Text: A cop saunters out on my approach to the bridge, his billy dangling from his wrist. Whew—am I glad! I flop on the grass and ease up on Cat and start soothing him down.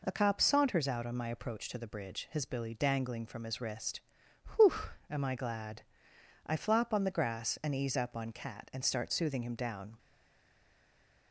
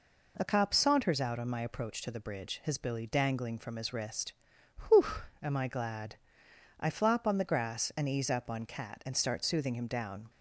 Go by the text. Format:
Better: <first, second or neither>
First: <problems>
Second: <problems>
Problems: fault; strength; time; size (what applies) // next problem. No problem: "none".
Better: second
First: stays silent after the last word; noticeable; from 9.9 s on; 1.4 s long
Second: none